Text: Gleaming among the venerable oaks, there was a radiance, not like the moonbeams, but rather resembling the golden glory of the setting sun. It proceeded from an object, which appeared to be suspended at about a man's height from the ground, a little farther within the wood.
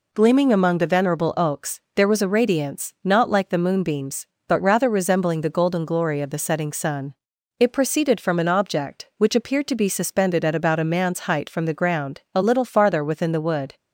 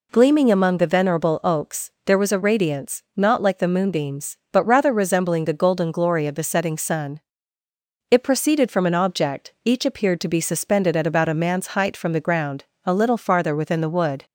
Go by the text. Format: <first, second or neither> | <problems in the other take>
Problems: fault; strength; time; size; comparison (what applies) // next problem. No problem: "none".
first | says "each" for "which"; at 9.6 s